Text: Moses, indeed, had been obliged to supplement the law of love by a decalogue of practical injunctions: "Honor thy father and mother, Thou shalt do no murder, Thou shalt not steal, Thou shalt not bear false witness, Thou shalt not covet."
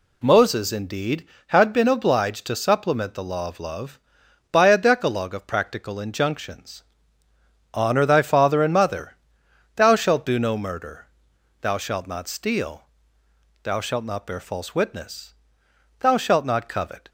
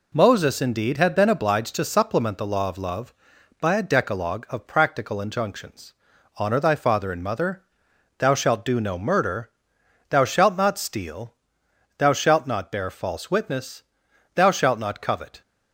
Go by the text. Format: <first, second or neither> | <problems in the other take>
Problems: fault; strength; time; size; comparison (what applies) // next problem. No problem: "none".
neither | none